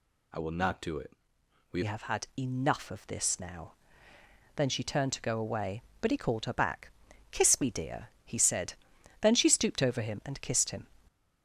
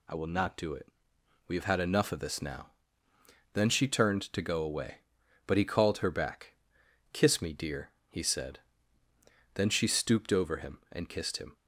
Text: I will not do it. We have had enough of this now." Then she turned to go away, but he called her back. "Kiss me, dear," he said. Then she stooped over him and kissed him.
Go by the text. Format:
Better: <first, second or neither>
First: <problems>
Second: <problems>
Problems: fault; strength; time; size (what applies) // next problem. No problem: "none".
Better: second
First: changes voice at "have"; from 1.8 s on; 9.0 s long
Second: none